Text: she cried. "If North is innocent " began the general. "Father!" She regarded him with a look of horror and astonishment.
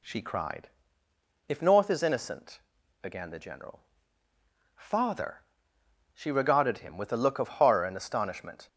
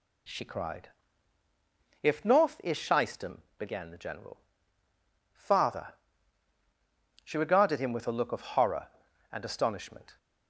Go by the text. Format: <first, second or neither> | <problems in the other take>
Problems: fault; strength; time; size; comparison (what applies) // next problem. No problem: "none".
first | says "shystem" for "innocent"; at 2.7 s